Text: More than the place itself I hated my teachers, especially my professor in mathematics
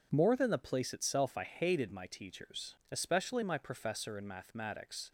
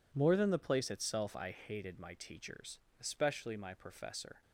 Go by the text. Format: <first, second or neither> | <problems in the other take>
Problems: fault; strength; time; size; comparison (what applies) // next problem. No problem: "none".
first | stops before "in mathematics"; at 4.4 s